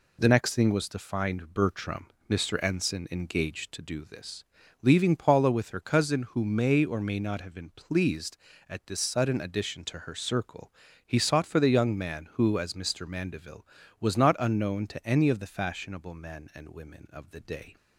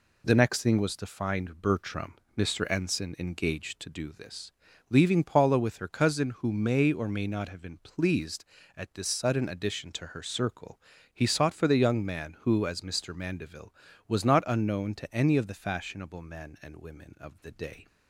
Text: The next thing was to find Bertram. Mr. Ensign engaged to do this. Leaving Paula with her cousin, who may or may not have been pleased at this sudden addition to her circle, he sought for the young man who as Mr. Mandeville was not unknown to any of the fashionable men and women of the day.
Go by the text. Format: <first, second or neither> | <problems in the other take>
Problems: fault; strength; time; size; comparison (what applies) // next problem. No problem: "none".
neither | none